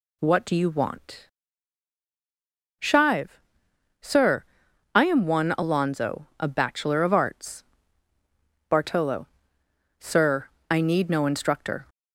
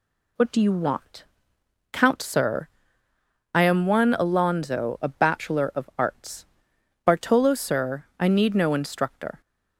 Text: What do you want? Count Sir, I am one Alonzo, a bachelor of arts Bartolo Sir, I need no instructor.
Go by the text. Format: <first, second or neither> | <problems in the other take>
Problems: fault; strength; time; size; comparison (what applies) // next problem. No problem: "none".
second | says "Shive" for "Count"; at 2.8 s // pauses between "arts" and "Bartolo"; at 7.6 s; 1.0 s long; noticeable in the second // pauses between "Bartolo" and "Sir"; noticeable; at 9.2 s; 0.74 s long